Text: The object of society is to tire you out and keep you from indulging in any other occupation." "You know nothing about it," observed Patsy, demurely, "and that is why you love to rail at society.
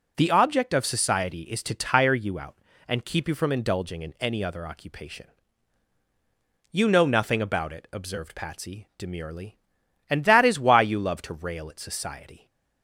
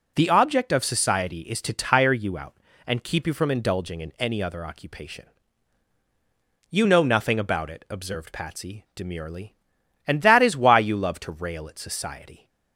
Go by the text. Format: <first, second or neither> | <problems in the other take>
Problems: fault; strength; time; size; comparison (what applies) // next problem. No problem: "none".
neither | none